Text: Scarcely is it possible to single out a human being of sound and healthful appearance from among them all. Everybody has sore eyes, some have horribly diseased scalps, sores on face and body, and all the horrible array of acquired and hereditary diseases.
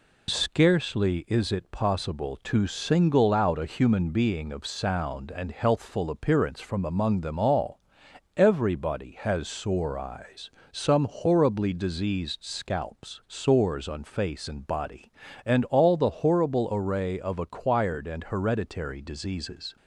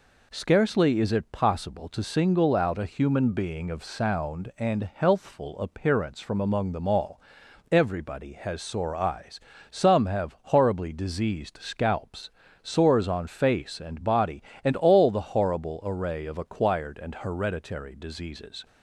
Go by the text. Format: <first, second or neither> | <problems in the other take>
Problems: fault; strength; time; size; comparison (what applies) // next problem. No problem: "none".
second | skips "have"; at 11.0 s